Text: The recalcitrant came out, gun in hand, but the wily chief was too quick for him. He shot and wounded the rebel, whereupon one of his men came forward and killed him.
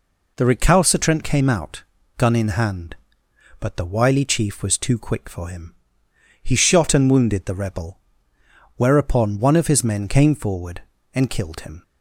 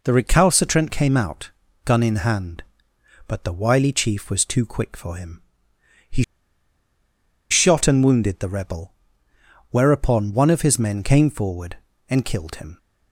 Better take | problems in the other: first | pauses between "He" and "shot"; strong; at 6.2 s; 1.2 s long

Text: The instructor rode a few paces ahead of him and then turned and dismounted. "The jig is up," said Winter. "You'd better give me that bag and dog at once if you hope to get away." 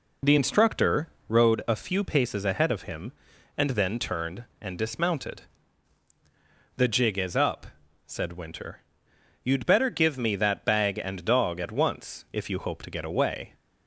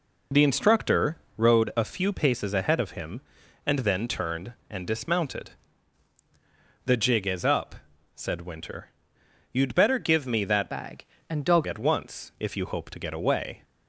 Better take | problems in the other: first | pauses between "instructor" and "rode"; slight; at 1.1 s; 0.18 s long; slight in the first // changes voice from "bag" to "dog"; from 10.7 to 11.6 s; 0.9 s long

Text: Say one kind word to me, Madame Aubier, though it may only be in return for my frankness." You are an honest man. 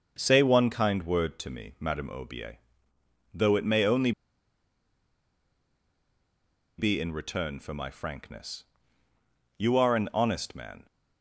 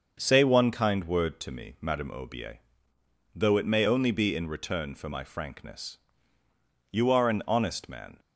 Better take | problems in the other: second | starts louder than the rest; until 1.1 s; 6.5 dB; also in the second // pauses between "only" and "be"; strong; at 4.1 s; 2.6 s long

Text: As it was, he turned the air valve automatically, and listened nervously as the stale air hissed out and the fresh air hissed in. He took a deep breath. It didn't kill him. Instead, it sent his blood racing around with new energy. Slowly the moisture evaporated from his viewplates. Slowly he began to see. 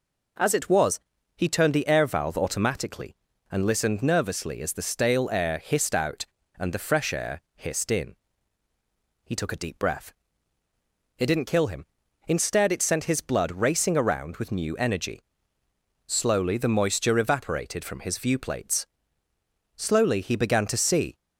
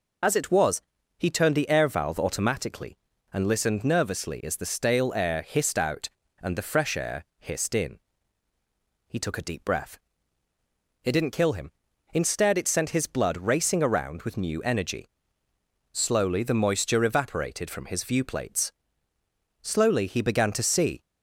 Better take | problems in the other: first | loses the start of "As"; at 0.2 s; 40 ms

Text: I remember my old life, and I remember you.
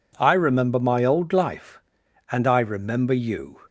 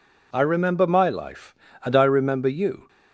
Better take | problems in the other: first | skips "old"; at 1.0 s

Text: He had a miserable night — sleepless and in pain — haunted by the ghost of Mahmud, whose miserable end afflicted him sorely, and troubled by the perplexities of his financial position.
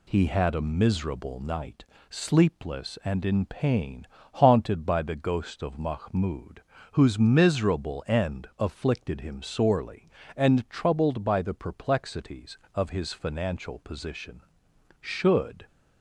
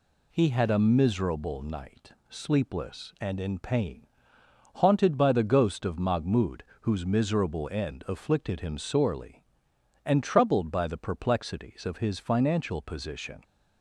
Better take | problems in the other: second | goes on to say "Should"; noticeable; from 15.0 s on; 0.64 s long

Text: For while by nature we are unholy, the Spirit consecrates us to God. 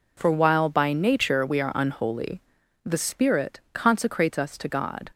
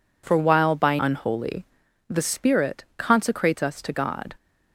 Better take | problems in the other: first | skips "nature we are"; at 0.9 s

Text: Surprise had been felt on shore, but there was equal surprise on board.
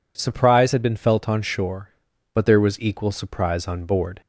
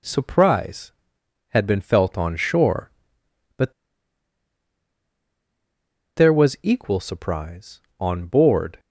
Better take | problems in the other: first | pauses between "but" and "there"; strong; at 3.7 s; 2.4 s long

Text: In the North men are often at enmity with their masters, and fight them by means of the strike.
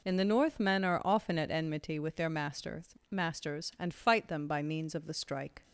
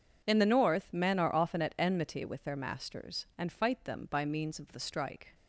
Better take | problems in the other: second | says "masters" twice; at 3.1 s

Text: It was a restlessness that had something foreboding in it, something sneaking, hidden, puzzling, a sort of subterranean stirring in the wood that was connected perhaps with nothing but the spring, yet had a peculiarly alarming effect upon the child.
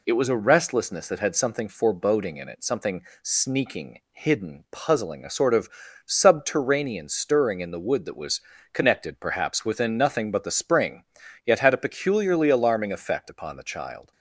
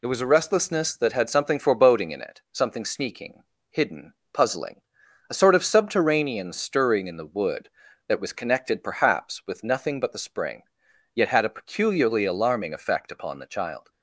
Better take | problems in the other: second | pauses between "something" and "sneaking"; slight; at 3.0 s; 0.22 s long // pauses between "of" and "subterranean"; at 5.6 s; 0.38 s long // pauses between "was" and "connected"; slight; at 8.3 s; 0.32 s long // says "within" for "with"; at 9.6 s

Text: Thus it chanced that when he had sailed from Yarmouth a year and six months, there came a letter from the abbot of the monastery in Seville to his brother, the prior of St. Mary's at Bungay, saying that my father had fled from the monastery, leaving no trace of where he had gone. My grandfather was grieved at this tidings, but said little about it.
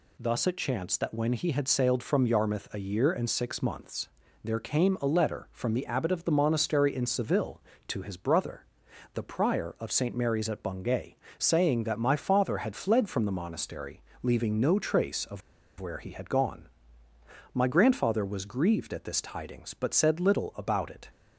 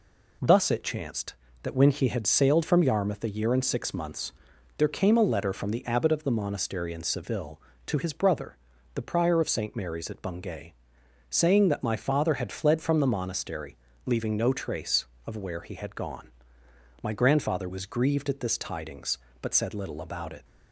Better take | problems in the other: second | pauses between "of" and "where"; at 15.4 s; 0.39 s long

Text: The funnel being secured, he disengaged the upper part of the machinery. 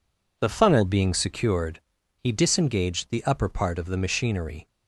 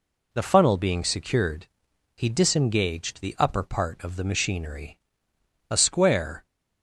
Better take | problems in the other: first | goes on to say "A square"; noticeable; from 5.6 s on; 0.76 s long

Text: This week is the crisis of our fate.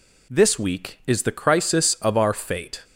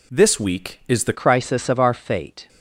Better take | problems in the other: first | changes voice at "crisis"; from 1.1 s on; 1.3 s long

